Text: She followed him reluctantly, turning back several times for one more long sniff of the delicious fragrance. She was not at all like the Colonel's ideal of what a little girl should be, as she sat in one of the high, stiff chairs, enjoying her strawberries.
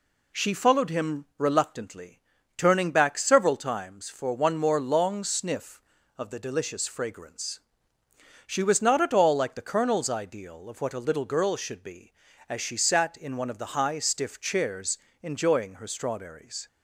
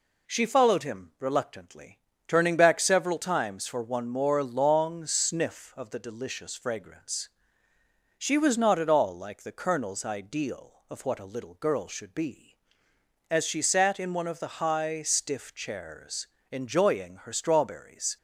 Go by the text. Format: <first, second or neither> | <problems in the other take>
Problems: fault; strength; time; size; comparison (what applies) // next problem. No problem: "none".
neither | none